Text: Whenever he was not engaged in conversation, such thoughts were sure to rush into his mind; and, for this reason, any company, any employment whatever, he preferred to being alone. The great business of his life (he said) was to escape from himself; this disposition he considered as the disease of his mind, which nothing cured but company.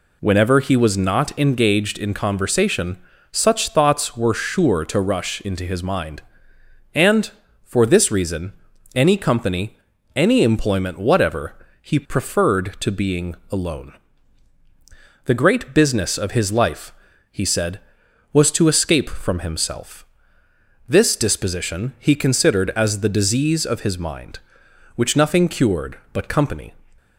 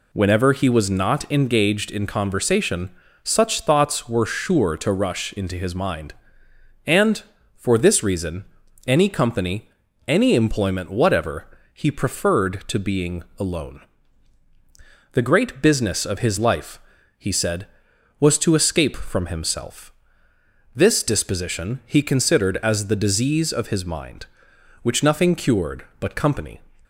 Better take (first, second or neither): neither